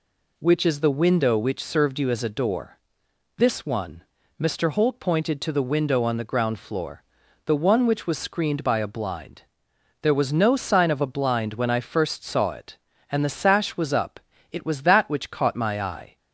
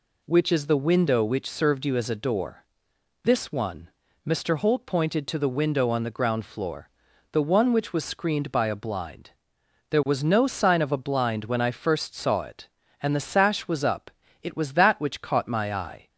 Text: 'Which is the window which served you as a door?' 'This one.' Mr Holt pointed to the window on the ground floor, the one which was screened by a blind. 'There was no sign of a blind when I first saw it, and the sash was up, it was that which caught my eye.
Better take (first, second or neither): neither